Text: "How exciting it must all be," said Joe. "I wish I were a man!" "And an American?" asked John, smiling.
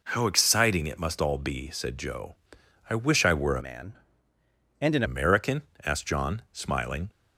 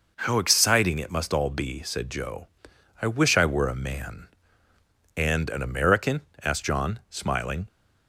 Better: second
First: changes voice from "man" to "an"; from 3.6 to 5.0 s; 1.4 s long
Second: none

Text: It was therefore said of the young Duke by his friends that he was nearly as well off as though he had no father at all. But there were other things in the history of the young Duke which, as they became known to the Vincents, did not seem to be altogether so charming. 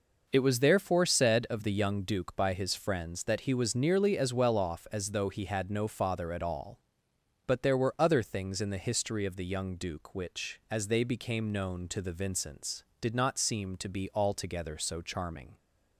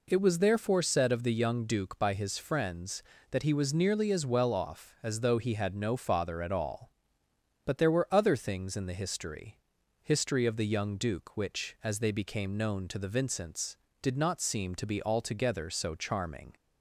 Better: first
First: none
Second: says "history" twice; at 10.0 s

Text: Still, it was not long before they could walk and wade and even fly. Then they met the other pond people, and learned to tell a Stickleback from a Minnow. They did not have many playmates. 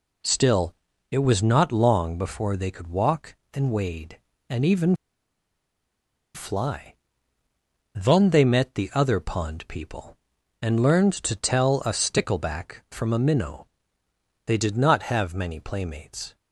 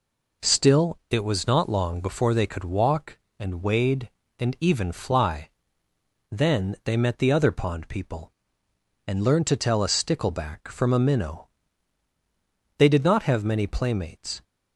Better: second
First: pauses between "even" and "fly"; strong; at 4.9 s; 1.3 s long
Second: none

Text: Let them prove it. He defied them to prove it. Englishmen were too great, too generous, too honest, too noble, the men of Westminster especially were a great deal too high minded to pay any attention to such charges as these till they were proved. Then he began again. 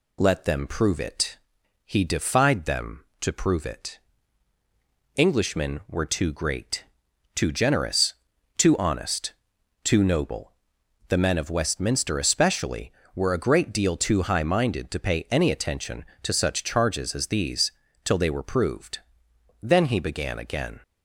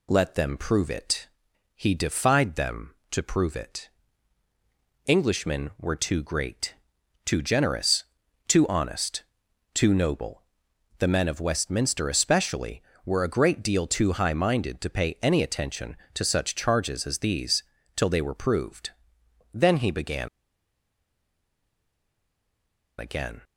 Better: first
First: pauses between "these" and "till"; slight; at 17.7 s; 0.32 s long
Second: pauses between "these" and "till"; slight; at 17.6 s; 0.32 s long // pauses between "began" and "again"; strong; at 20.2 s; 2.7 s long

